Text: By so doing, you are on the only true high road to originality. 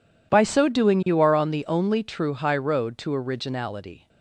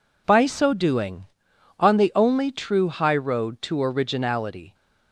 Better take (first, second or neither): first